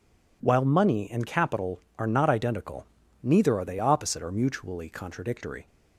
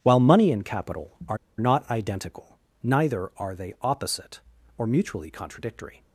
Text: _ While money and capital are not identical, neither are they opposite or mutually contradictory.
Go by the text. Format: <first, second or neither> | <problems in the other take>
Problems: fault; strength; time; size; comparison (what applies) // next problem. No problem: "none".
first | pauses between "are" and "not"; slight; at 1.3 s; 0.21 s long